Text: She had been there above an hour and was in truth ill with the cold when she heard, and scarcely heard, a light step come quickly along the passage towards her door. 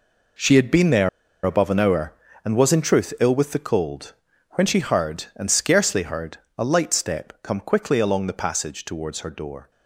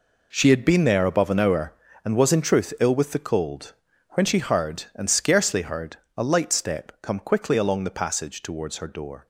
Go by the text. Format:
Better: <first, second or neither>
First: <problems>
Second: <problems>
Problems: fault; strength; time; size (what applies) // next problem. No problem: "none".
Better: second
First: pauses between "there" and "above"; at 1.0 s; 0.37 s long // pauses between "cold" and "when"; at 4.1 s; 0.40 s long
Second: pauses between "cold" and "when"; at 3.7 s; 0.39 s long